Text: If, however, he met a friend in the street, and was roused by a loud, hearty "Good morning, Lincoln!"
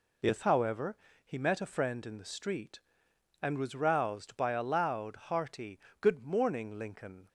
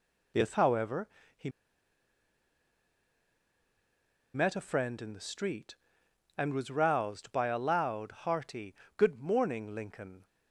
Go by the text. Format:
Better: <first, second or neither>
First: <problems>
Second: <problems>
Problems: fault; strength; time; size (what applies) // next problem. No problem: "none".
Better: first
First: pauses between "hearty" and "Good"; slight; at 5.7 s; 0.21 s long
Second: pauses between "he" and "met"; strong; at 1.4 s; 2.8 s long // pauses between "hearty" and "Good"; slight; at 8.7 s; 0.22 s long